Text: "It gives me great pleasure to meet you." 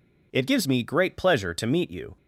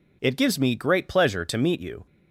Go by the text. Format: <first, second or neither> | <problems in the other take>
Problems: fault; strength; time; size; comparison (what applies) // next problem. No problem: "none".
neither | none